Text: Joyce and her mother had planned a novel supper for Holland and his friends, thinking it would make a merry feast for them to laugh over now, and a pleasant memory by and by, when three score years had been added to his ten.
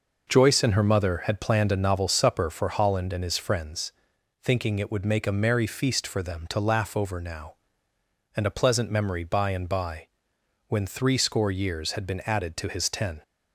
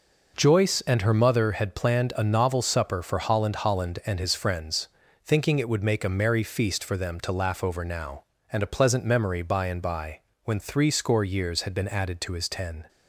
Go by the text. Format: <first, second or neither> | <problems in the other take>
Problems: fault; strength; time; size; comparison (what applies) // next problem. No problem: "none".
first | says "Holland" twice; at 3.5 s